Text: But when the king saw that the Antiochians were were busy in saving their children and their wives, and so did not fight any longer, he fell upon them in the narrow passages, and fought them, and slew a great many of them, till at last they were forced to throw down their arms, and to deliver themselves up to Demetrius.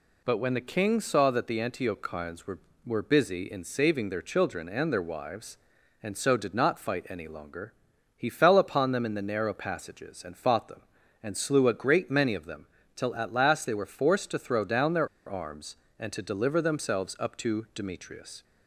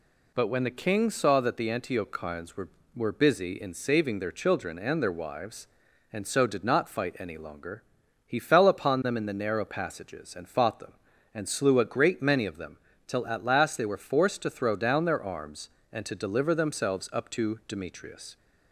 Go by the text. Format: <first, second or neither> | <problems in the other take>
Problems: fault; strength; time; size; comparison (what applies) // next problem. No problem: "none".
second | pauses between "their" and "arms"; slight; at 15.0 s; 0.19 s long